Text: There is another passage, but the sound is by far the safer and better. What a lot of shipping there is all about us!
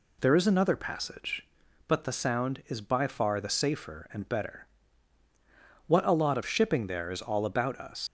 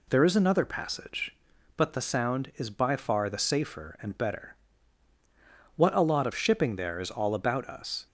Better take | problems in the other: second | leaves "us" unfinished; at 8.0 s; 105 ms

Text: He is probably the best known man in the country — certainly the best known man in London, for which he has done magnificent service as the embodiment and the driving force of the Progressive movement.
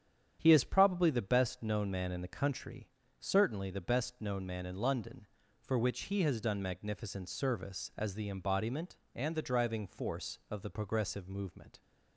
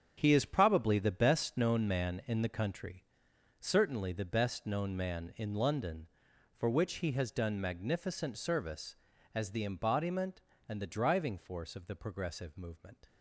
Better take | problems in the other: first | gets quieter; strong; throughout; 11.5 dB // starts louder than the rest; strong; until 1.1 s; 8 dB; strong in the first

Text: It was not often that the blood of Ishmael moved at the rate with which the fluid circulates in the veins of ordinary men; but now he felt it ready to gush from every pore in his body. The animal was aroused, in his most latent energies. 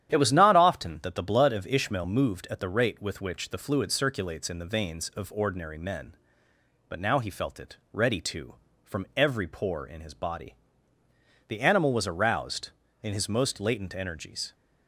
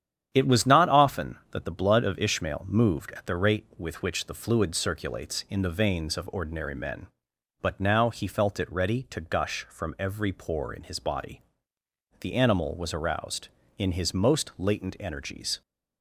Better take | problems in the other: second | starts louder than the rest; strong; until 1.1 s; 10.5 dB; strong in the second // pauses between "it" and "ready"; slight; at 7.7 s; 0.16 s long // skips "gush"; at 8.6 s

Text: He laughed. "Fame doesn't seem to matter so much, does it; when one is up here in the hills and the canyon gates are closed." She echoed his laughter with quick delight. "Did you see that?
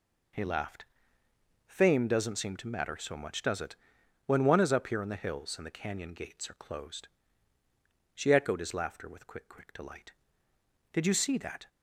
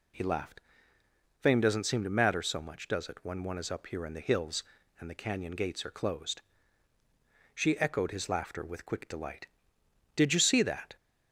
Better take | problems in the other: second | says "quick" twice; at 9.4 s

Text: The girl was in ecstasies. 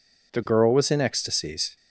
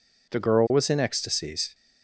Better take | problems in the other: neither | none

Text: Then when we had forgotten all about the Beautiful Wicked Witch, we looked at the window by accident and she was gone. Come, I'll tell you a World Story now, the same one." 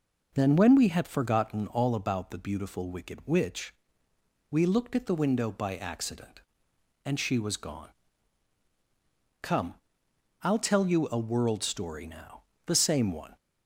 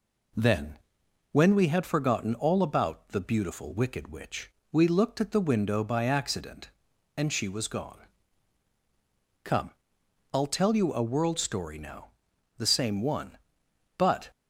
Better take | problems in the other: first | pauses between "Then" and "when"; noticeable; at 0.7 s; 0.54 s long // goes on to say "But"; slight; from 13.9 s on; 0.34 s long

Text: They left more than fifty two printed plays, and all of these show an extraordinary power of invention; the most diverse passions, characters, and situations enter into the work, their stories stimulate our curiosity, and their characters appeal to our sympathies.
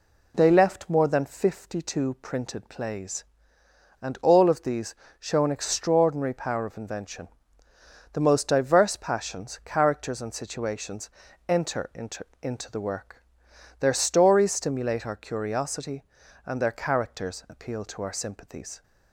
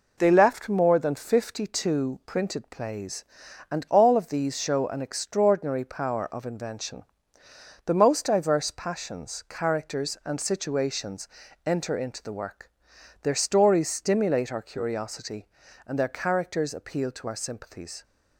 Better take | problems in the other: second | pauses between "these" and "show"; slight; at 4.9 s; 0.24 s long // pauses between "situations" and "enter"; at 11.0 s; 0.40 s long; slight in the second // says "into" twice; at 12.4 s

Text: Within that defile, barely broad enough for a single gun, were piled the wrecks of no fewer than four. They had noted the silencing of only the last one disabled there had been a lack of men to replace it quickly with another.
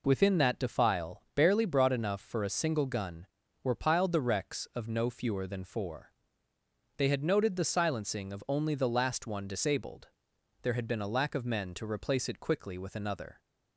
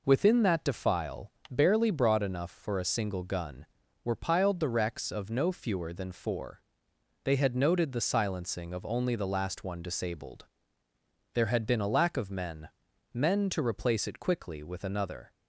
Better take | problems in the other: first | pauses between "disabled" and "there"; noticeable; at 10.4 s; 0.86 s long; noticeable in the first // says "men" twice; at 13.1 s

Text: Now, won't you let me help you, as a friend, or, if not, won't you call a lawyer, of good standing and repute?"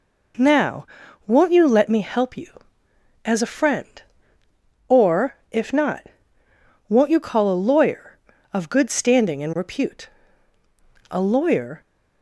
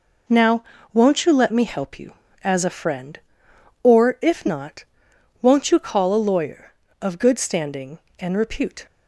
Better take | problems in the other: second | goes on to say "A lawyer"; noticeable; from 11.0 s on; 0.72 s long

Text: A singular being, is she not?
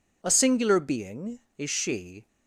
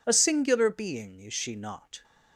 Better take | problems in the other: second | stops before "not"; at 2.2 s

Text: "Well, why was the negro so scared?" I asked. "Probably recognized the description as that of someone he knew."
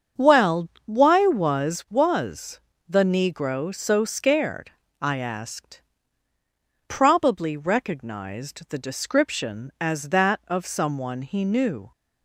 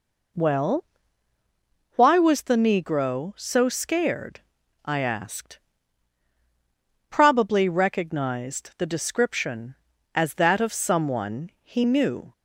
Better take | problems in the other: second | starts louder than the rest; strong; until 1.3 s; 7 dB // says "was" twice; at 1.8 s

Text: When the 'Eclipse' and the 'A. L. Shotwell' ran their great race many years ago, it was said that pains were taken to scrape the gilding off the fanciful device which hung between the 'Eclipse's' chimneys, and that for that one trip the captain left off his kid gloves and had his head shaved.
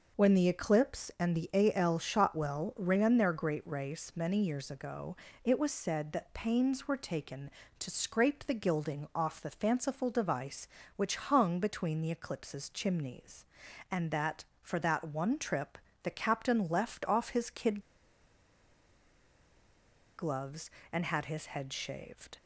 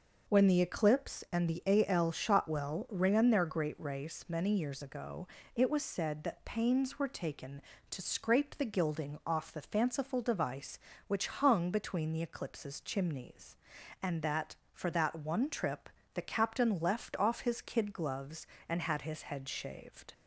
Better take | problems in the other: second | pauses between "trip" and "the"; slight; at 15.7 s; 0.24 s long; slight in the second // pauses between "kid" and "gloves"; strong; at 17.7 s; 2.3 s long

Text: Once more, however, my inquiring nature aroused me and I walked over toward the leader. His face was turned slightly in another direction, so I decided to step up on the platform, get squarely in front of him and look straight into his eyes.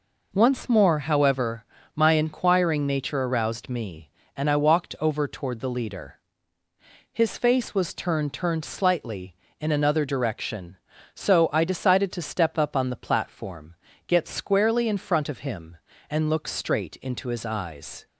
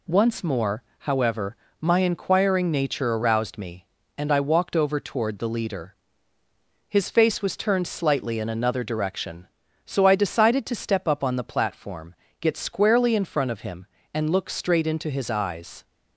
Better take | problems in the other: second | says "turned" twice; at 8.3 s

